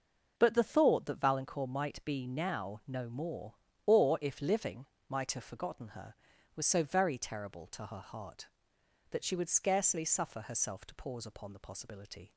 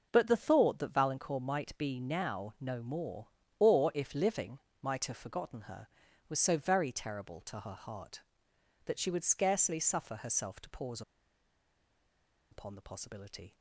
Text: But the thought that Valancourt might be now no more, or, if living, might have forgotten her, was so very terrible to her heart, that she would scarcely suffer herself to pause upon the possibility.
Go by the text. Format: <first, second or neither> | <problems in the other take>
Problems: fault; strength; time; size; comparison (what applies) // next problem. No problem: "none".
first | pauses between "pause" and "upon"; strong; at 11.0 s; 1.5 s long